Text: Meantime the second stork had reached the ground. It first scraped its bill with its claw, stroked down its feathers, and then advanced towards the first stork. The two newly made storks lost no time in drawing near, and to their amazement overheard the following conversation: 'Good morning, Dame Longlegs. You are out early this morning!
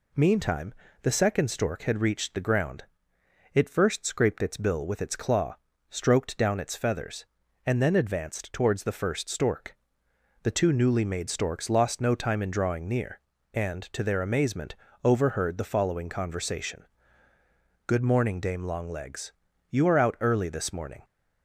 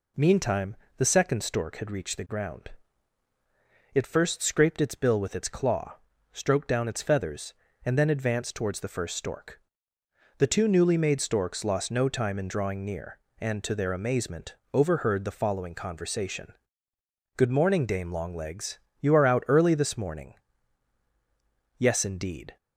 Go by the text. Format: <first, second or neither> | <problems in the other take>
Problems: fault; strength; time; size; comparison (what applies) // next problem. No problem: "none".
first | pauses between "Meantime" and "the"; slight; at 0.7 s; 0.20 s long; slight in the first // pauses between "amazement" and "overheard"; slight; at 14.5 s; 0.18 s long; slight in the first // goes on to say "Yes indeed"; noticeable; from 21.7 s on; 0.80 s long